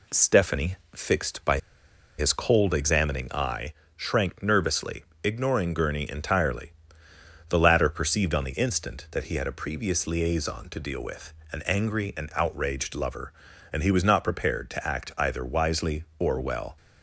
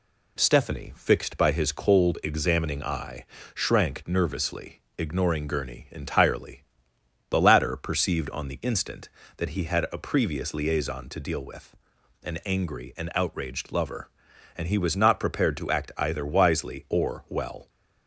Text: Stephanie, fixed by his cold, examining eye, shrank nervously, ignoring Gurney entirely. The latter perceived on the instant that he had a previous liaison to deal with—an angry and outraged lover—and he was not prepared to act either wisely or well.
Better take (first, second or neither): second